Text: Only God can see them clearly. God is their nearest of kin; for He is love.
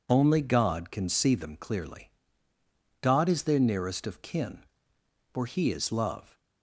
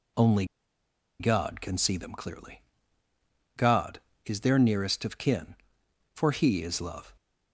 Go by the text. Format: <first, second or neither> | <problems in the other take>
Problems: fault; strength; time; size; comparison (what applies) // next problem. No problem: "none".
first | pauses between "Only" and "God"; noticeable; at 0.4 s; 0.75 s long